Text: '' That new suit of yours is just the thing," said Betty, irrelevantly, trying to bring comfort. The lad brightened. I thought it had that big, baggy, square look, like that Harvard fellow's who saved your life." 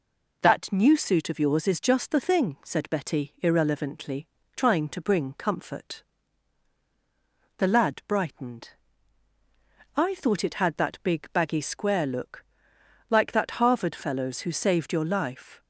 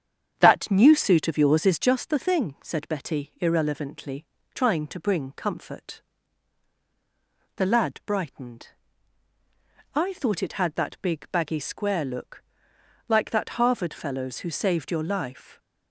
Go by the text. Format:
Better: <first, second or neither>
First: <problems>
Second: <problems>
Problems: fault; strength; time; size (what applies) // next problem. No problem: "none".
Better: first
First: none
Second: starts louder than the rest; strong; until 2.0 s; 8 dB